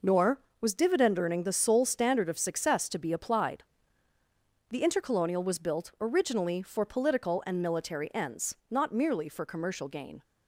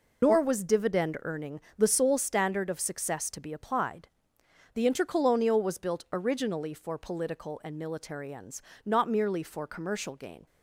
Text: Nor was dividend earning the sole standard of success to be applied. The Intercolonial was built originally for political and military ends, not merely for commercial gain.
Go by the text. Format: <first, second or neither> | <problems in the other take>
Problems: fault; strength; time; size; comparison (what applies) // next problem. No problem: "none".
first | loses the start of "Nor"; at 0.2 s; 90 ms // pauses between "earning" and "the"; slight; at 1.5 s; 0.18 s long